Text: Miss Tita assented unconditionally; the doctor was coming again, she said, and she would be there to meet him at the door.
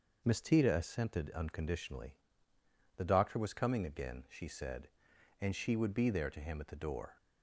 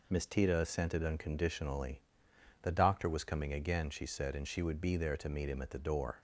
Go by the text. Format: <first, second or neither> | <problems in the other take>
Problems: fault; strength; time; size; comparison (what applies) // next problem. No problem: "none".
second | skips "meet"; at 6.3 s